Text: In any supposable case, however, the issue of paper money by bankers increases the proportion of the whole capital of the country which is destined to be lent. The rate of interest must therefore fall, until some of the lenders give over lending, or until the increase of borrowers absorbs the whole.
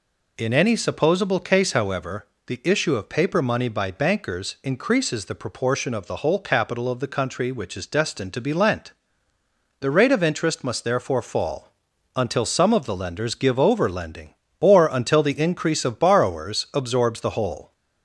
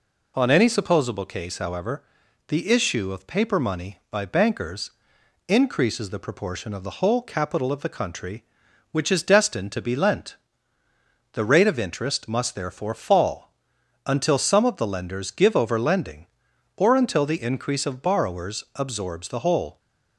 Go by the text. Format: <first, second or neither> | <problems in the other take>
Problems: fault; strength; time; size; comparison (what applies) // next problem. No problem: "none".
first | says "On" for "In"; at 0.3 s // pauses between "bankers" and "increases"; noticeable; at 4.8 s; 0.58 s long